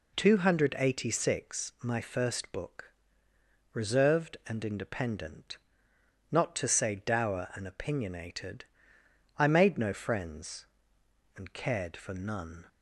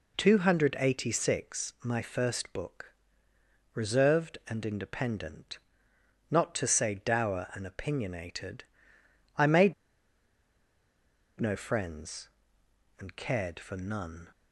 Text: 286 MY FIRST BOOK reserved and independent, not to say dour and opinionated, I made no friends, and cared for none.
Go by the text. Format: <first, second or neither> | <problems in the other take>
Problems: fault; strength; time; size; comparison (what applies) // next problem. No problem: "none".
first | pauses between "BOOK" and "reserved"; noticeable; at 2.9 s; 0.82 s long; noticeable in the first // pauses between "made" and "no"; strong; at 9.7 s; 1.6 s long